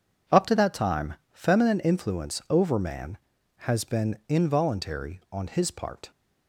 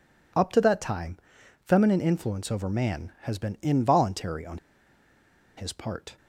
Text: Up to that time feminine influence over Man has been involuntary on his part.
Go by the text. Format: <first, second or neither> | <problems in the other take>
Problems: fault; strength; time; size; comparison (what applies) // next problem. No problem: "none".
first | pauses between "time" and "feminine"; noticeable; at 1.1 s; 0.46 s long; slight in the first // pauses between "on" and "his"; at 4.5 s; 1.0 s long